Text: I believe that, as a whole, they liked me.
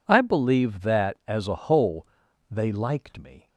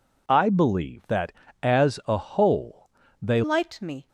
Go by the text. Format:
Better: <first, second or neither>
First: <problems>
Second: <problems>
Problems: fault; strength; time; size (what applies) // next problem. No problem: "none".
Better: first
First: none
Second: changes voice at "liked"; from 3.4 s on; 0.6 s long